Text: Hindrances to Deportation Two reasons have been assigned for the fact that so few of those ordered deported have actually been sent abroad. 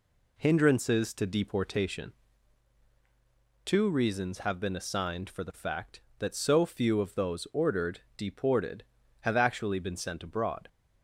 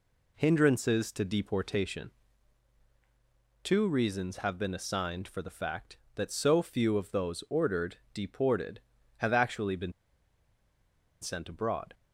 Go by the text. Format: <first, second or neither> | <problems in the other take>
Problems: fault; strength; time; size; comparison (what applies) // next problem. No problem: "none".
first | pauses between "Deportation" and "Two"; strong; at 2.1 s; 1.5 s long; strong in the first // pauses between "been" and "sent"; strong; at 9.9 s; 1.2 s long